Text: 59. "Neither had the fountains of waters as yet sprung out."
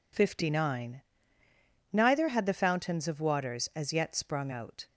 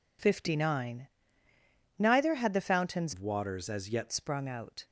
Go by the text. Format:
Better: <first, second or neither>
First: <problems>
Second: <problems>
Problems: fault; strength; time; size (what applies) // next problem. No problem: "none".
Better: first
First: none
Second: changes voice from "of" to "yet"; from 3.1 to 4.1 s; 1.0 s long